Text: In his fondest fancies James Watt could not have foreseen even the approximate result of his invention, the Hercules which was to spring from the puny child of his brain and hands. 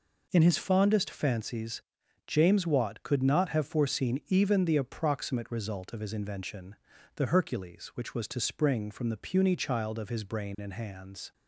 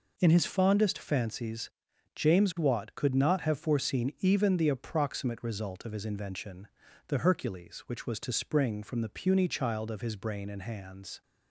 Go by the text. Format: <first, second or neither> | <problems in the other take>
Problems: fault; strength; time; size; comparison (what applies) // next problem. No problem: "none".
neither | pauses between "fancies" and "James"; noticeable; the same in both